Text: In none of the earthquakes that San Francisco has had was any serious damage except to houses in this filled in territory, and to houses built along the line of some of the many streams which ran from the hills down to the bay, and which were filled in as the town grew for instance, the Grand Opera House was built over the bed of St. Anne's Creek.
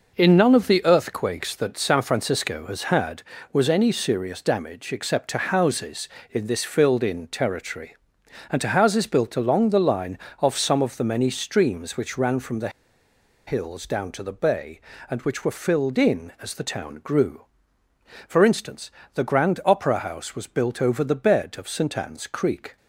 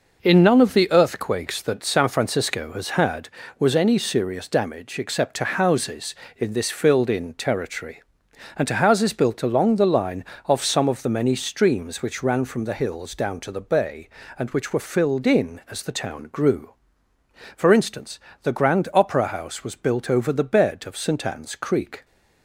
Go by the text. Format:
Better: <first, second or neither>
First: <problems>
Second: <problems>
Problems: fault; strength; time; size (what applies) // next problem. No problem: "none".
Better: second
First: pauses between "the" and "hills"; noticeable; at 12.6 s; 0.77 s long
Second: none